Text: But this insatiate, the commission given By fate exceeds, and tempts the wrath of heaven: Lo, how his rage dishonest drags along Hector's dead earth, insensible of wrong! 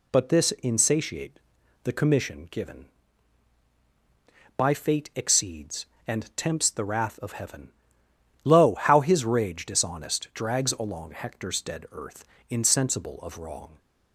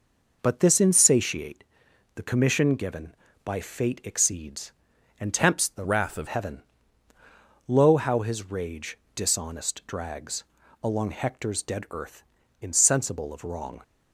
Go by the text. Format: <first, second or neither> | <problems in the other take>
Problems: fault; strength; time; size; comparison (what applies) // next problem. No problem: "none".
first | changes voice from "wrath" to "of"; from 5.8 to 6.2 s; 0.4 s long // pauses between "rage" and "dishonest"; slight; at 8.9 s; 0.20 s long // pauses between "drags" and "along"; at 10.4 s; 0.40 s long